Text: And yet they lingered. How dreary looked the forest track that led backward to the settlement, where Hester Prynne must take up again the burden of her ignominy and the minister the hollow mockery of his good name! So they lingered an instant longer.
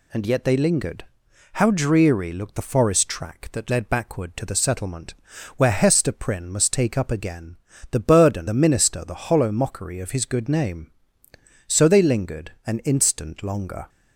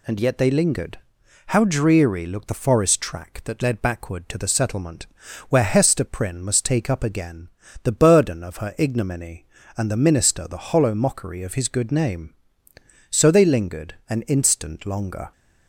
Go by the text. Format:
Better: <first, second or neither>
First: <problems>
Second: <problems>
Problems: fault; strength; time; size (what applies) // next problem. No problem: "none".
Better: second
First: pauses between "again" and "the"; slight; at 7.5 s; 0.34 s long // skips "of her ignominy and"; at 8.4 s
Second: pauses between "again" and "the"; slight; at 7.4 s; 0.34 s long